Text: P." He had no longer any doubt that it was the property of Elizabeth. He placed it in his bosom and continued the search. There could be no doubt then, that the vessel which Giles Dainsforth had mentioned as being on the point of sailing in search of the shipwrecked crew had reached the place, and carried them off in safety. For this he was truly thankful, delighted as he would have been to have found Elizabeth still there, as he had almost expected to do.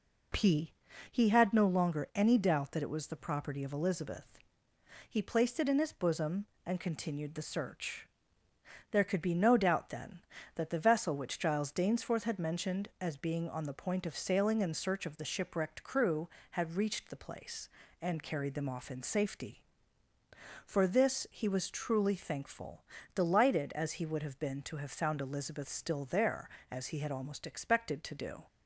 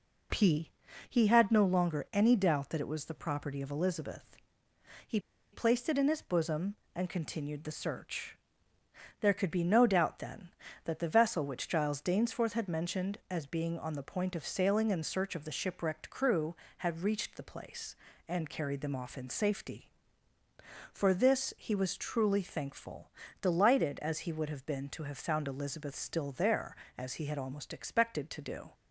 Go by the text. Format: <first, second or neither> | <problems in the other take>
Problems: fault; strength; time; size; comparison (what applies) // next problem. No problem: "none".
first | pauses between "He" and "placed"; slight; at 5.1 s; 0.33 s long